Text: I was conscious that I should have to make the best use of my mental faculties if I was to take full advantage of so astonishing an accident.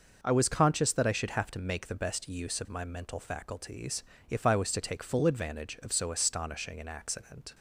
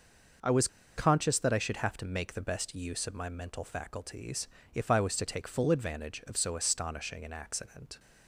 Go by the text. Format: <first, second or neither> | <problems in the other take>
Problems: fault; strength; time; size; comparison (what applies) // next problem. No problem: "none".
first | pauses between "was" and "conscious"; slight; at 0.6 s; 0.29 s long // pauses between "faculties" and "if"; slight; at 4.4 s; 0.24 s long; slight in the first